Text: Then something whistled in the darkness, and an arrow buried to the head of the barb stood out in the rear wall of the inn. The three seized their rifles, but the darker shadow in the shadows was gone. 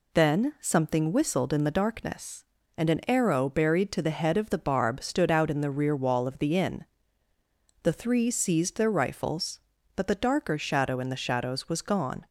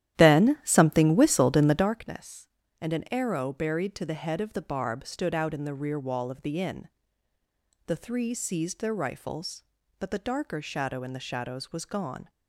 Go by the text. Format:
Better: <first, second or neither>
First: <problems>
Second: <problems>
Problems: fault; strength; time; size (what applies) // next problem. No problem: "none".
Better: first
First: none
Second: starts louder than the rest; strong; until 2.0 s; 12 dB